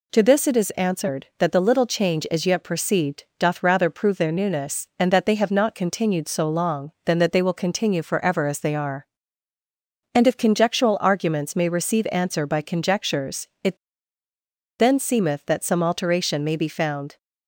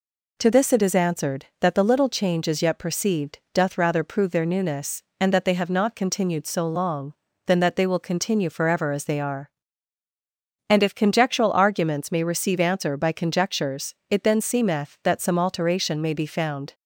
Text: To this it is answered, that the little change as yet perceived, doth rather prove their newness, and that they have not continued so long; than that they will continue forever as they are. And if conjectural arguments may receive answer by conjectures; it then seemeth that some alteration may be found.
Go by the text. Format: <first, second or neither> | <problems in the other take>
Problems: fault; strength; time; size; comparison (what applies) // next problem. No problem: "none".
second | pauses between "it" and "then"; at 13.7 s; 1.0 s long